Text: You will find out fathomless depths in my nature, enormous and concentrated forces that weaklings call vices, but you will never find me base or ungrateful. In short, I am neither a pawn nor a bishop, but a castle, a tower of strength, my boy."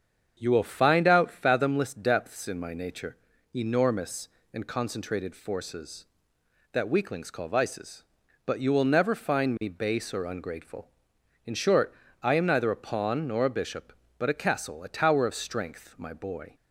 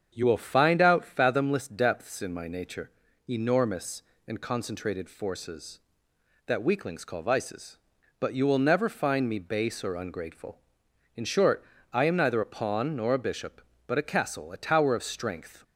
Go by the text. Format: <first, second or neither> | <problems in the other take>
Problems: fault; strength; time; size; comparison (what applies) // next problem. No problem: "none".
first | starts louder than the rest; strong; until 1.1 s; 7.5 dB; strong in the first // stops before "my boy"; at 15.6 s